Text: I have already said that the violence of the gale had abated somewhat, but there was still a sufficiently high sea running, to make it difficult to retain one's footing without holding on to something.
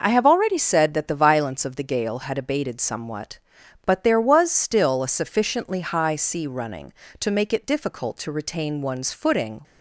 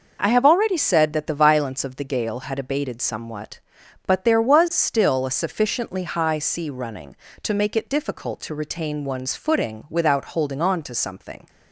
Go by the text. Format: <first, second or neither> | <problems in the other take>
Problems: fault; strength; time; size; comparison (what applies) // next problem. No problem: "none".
second | stops before "without holding on to something"; at 9.6 s